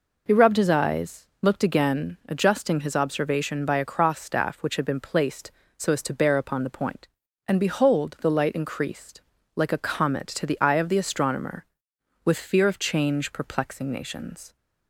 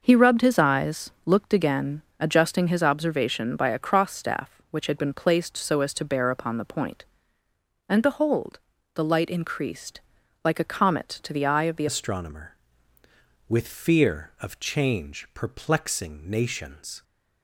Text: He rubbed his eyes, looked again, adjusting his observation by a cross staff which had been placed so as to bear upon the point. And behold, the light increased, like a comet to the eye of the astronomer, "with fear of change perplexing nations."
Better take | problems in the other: first | changes voice at "astronomer"; from 11.8 s on; 5.2 s long

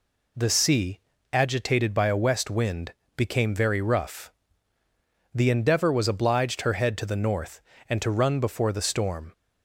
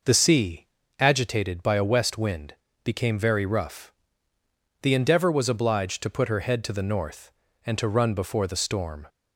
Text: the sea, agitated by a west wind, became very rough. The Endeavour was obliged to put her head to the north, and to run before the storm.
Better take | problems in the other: second | skips "to put"; at 6.6 s

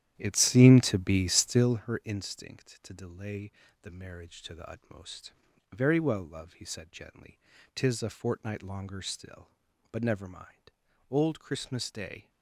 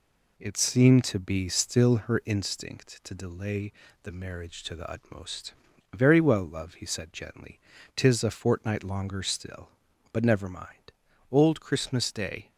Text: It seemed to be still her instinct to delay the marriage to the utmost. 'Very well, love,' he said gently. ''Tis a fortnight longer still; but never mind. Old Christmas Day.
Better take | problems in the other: second | starts louder than the rest; strong; until 1.8 s; 11.5 dB // pauses between "delay" and "the"; slight; at 3.5 s; 0.30 s long; slight in the second

